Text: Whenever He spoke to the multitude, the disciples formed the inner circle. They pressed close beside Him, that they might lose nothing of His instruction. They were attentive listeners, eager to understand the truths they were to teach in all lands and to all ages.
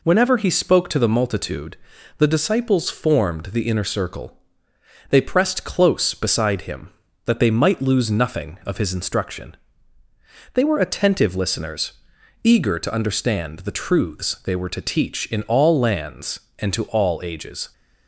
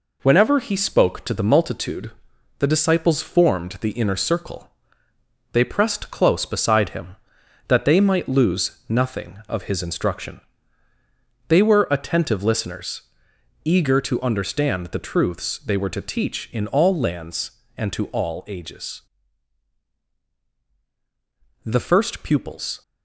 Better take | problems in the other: first | goes on to say "The first pupils"; noticeable; from 21.6 s on; 1.1 s long

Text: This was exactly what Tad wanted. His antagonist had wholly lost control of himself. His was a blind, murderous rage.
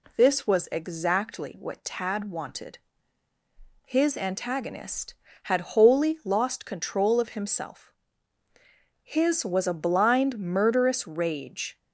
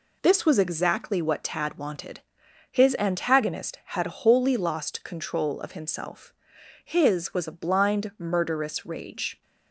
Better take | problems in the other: neither | none

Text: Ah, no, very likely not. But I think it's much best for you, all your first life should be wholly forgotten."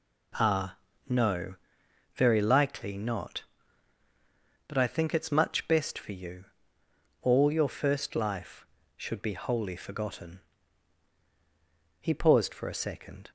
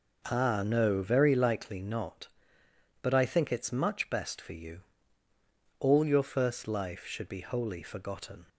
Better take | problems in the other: second | goes on to say "He paused for a second"; noticeable; from 11.9 s on; 1.3 s long

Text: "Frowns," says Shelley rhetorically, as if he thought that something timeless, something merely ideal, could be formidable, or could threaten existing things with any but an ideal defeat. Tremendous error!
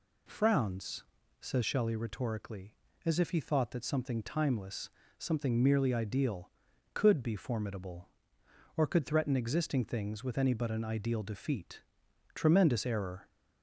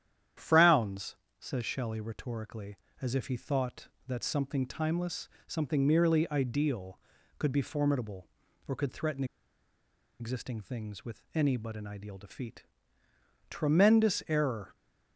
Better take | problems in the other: first | starts louder than the rest; strong; until 1.6 s; 10 dB // pauses between "threaten" and "existing"; noticeable; at 9.2 s; 0.95 s long

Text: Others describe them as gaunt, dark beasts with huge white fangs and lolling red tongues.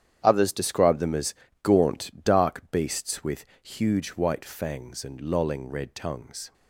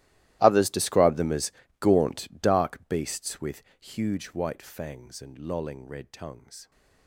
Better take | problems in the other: first | gets quieter; strong; throughout; 22 dB // starts louder than the rest; strong; until 1.4 s; 15.5 dB; strong in the first // pauses between "as" and "gaunt"; slight; at 1.5 s; 0.30 s long; slight in the first // pauses between "with" and "huge"; slight; at 3.6 s; 0.16 s long; slight in the first

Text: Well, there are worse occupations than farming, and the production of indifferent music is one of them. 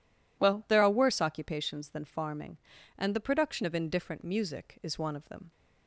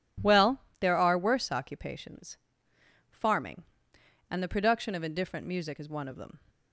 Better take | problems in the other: first | skips "than"; at 2.7 s

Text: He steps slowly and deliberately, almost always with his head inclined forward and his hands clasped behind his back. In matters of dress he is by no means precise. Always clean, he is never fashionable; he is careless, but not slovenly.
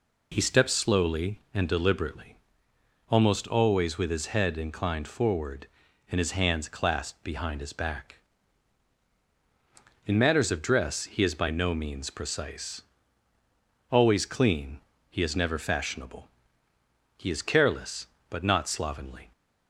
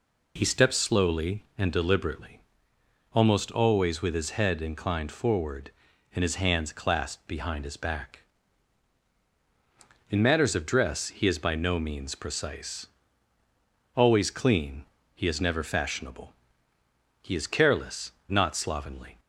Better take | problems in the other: first | skips "but"; at 18.1 s

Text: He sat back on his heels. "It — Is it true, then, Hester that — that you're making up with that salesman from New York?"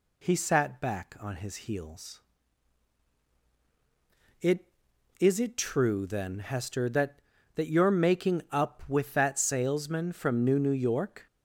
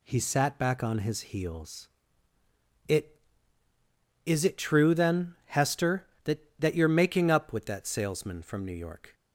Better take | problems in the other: second | says "New" twice; at 10.6 s

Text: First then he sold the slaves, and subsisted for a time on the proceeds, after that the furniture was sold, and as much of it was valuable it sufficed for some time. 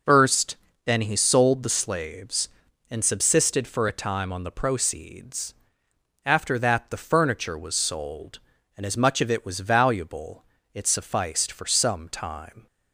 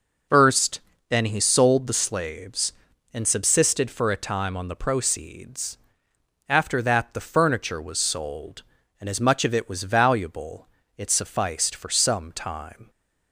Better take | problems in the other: neither | pauses between "First" and "then"; slight; the same in both // pauses between "valuable" and "it"; slight; the same in both

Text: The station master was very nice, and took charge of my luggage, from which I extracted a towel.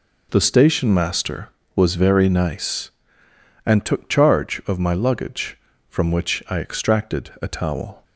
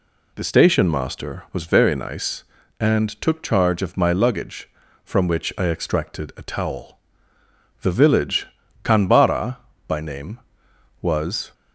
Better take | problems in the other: first | goes on to say "The village Kanbara by name was"; strong; from 7.8 s on; 3.7 s long

